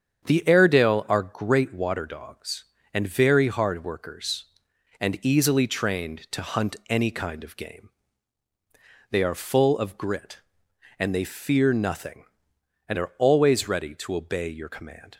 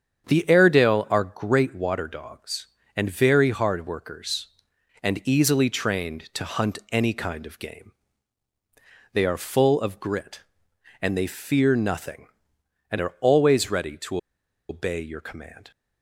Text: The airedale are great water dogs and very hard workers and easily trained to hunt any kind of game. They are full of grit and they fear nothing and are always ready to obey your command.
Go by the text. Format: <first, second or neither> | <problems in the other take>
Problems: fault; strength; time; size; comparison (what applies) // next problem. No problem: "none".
first | starts louder than the rest; strong; until 1.3 s; 8 dB; strong in the first // pauses between "to" and "obey"; noticeable; at 14.1 s; 0.52 s long